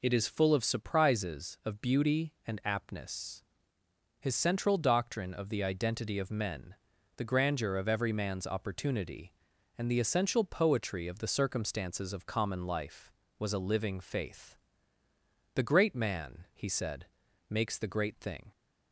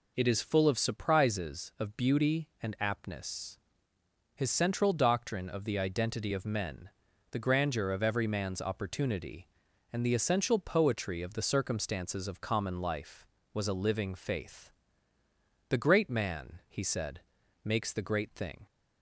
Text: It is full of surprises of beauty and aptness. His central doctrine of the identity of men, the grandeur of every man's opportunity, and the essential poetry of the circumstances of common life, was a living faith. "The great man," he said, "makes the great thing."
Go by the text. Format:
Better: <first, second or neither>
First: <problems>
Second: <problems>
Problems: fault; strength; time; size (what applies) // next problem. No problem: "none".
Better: neither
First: none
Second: none